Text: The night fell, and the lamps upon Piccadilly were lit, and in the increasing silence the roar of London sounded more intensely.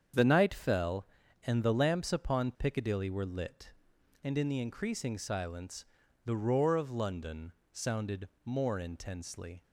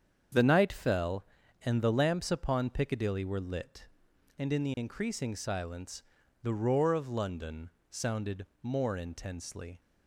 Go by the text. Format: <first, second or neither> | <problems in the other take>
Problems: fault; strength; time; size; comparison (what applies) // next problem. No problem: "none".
neither | starts louder than the rest; strong; the same in both // pauses between "silence" and "the"; the same in both // pauses between "London" and "sounded"; slight; the same in both // pauses between "sounded" and "more"; slight; the same in both